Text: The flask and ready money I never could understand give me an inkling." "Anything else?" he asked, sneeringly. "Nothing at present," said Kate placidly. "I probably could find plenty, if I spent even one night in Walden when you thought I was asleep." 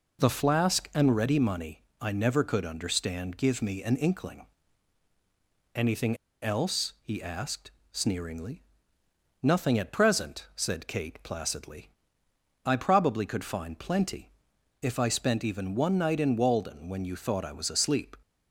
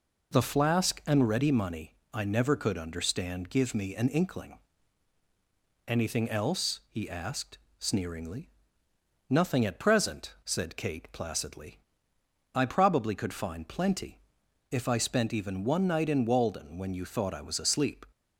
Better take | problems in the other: second | pauses between "money" and "I"; slight; at 1.7 s; 0.22 s long; slight in the second // pauses between "Anything" and "else"; slight; at 6.1 s; 0.26 s long

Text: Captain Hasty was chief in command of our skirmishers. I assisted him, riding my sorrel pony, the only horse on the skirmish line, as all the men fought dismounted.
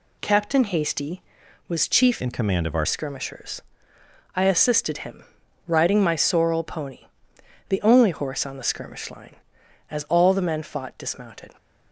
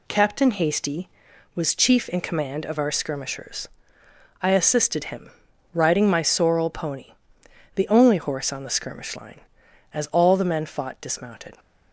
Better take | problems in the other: second | changes voice from "in" to "our"; from 2.1 to 2.8 s; 0.7 s long

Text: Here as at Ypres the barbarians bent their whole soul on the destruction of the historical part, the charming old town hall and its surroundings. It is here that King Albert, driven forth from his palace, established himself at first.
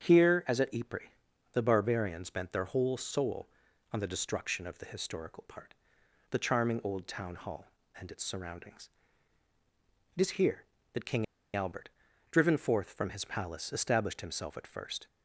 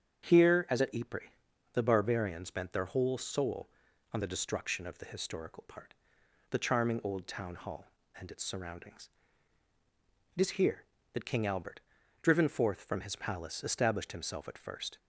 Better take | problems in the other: second | starts louder than the rest; strong; until 1.5 s; 8 dB; strong in the second // pauses between "Ypres" and "the"; noticeable; at 1.0 s; 0.46 s long; noticeable in the second // pauses between "King" and "Albert"; slight; at 11.2 s; 0.31 s long

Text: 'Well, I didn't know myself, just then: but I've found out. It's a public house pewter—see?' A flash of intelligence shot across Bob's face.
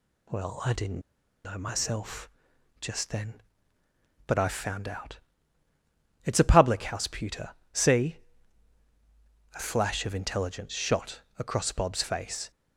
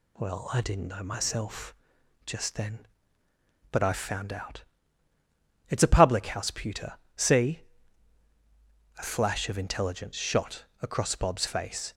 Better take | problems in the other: second | pauses between "didn't" and "know"; at 0.9 s; 0.45 s long // pauses between "shot" and "across"; slight; at 11.2 s; 0.16 s long; slight in the second

